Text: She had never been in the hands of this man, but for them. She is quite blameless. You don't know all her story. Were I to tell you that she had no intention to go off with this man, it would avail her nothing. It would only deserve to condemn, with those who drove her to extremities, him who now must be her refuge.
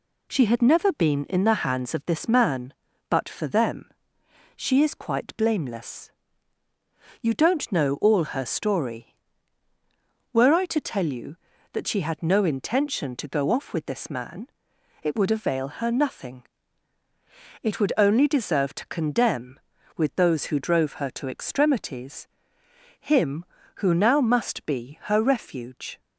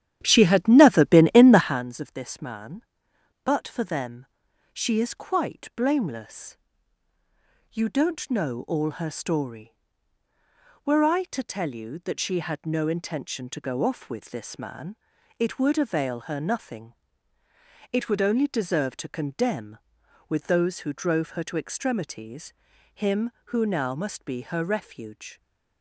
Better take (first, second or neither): first